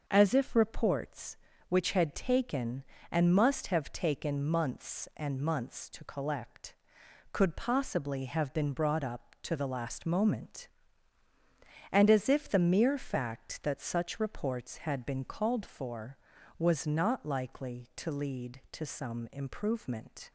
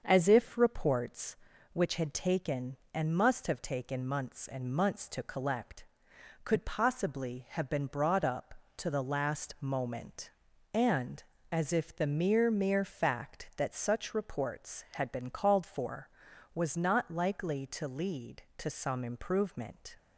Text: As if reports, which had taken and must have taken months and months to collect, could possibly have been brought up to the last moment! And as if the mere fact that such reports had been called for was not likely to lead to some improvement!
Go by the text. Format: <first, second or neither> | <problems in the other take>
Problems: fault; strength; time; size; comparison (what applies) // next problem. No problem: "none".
first | starts louder than the rest; until 1.0 s; 6.5 dB; also in the first // says "mere" twice; at 12.5 s